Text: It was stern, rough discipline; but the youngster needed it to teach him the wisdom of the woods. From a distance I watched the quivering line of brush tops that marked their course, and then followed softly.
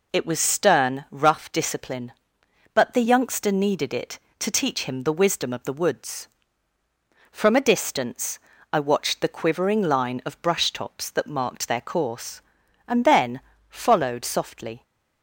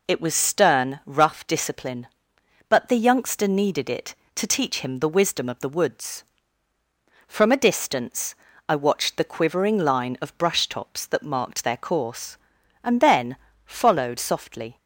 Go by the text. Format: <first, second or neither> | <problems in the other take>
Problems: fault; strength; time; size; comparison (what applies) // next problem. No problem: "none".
neither | pauses between "distance" and "I"; slight; the same in both // pauses between "then" and "followed"; slight; the same in both